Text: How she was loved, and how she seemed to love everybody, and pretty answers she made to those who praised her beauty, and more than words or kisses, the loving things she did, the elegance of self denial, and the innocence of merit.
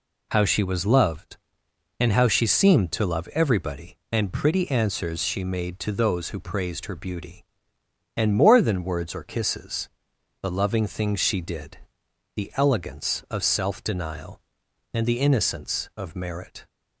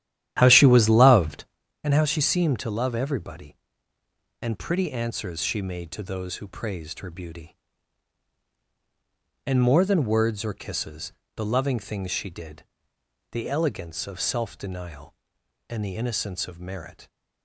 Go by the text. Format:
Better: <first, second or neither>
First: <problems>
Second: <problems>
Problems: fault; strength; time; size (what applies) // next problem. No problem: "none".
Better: first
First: none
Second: starts louder than the rest; strong; until 1.6 s; 11.5 dB